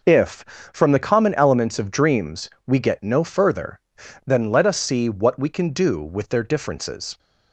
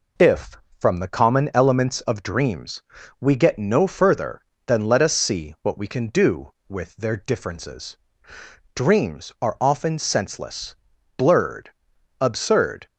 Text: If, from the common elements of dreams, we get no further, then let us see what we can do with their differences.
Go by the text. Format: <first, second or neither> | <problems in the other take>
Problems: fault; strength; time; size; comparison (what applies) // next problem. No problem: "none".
first | goes on to say "Dreams are often senseless blurred absurd"; strong; from 8.7 s on; 4.1 s long